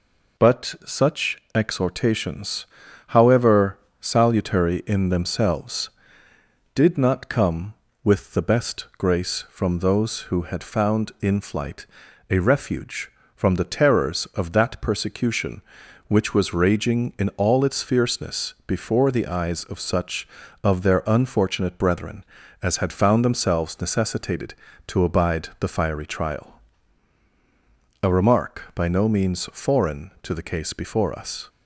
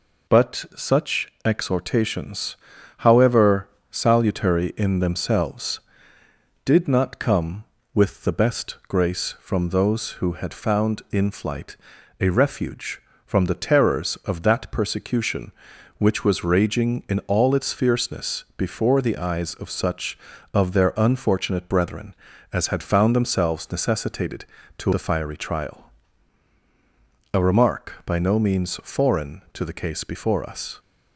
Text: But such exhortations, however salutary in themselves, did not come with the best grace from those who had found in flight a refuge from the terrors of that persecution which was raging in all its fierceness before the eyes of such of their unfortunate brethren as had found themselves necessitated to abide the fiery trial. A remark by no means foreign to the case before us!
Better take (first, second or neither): first